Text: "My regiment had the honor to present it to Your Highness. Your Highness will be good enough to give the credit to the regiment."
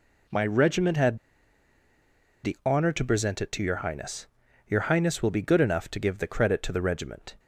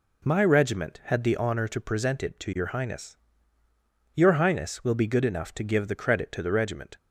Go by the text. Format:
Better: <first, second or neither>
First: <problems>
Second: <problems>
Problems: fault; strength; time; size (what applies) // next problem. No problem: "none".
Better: second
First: pauses between "had" and "the"; strong; at 1.1 s; 1.2 s long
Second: none